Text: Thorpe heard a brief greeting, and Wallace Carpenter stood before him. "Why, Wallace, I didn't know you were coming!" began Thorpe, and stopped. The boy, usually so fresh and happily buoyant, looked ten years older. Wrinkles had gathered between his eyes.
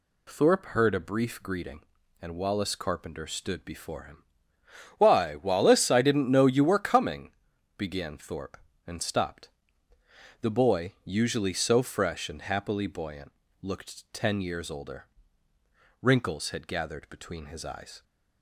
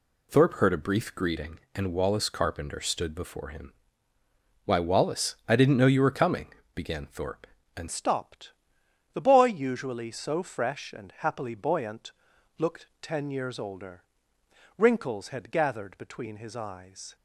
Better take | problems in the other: first | changes voice at "stopped"; from 7.8 s on; 9.3 s long

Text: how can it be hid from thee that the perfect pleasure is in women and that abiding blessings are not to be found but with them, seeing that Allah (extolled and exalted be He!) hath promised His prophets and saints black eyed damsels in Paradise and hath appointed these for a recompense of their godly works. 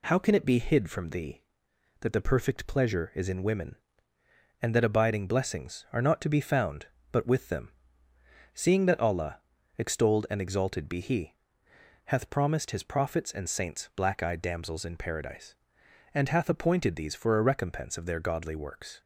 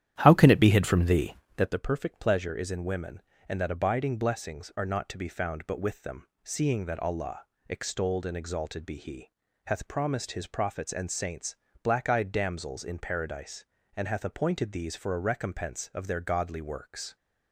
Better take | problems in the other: first | starts louder than the rest; strong; until 1.7 s; 11 dB // pauses between "saints" and "black"; slight; at 11.5 s; 0.26 s long

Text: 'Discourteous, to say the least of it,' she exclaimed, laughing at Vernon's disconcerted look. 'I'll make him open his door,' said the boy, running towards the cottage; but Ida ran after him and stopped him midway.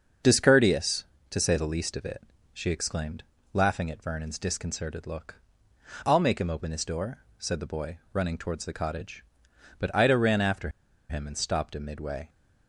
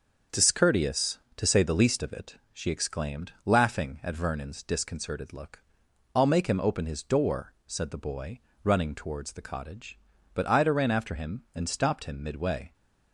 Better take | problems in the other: second | starts louder than the rest; until 1.5 s; 6.5 dB; also in the second // pauses between "after" and "him"; at 10.6 s; 0.41 s long

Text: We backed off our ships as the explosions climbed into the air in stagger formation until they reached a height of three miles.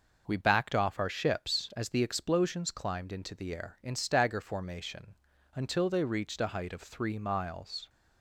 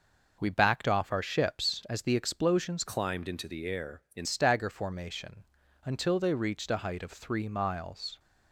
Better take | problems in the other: first | changes voice from "climbed" to "in"; from 2.8 to 4.2 s; 1.4 s long // pauses between "formation" and "until"; at 5.4 s; 0.38 s long; also in the first

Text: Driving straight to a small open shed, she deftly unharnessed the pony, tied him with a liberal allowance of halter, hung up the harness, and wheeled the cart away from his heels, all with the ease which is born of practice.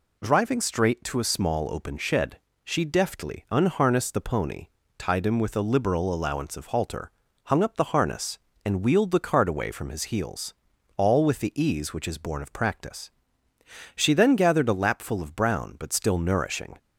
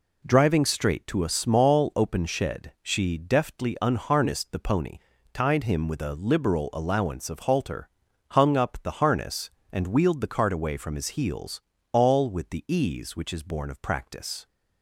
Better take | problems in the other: second | goes on to say "She then gathered a lapful of brown but still nourishing"; strong; from 13.9 s on; 2.8 s long

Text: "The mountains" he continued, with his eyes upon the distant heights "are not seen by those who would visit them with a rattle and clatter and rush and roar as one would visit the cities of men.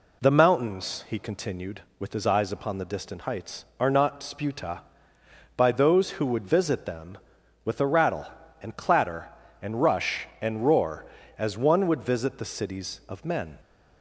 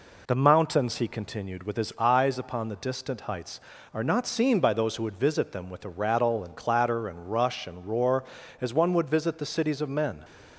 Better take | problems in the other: second | says "sputa" for "seen"; at 4.1 s

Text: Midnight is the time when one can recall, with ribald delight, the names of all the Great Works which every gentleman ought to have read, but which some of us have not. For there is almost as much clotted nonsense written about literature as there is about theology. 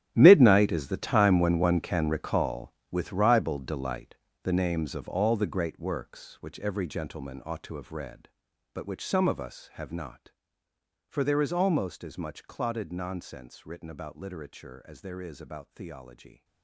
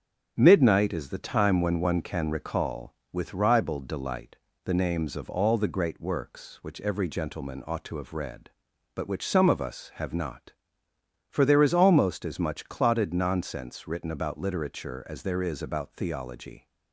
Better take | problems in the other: second | gets quieter; strong; throughout; 16 dB // starts louder than the rest; strong; until 1.1 s; 12 dB; strong in the second

